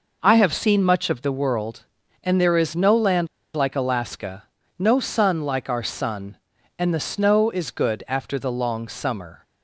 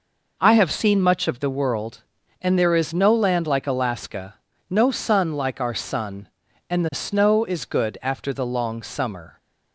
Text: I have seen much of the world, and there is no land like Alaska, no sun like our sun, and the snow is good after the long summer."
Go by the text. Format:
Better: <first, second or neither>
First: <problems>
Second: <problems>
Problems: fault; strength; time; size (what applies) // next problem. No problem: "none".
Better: second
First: pauses between "land" and "like"; slight; at 3.2 s; 0.29 s long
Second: none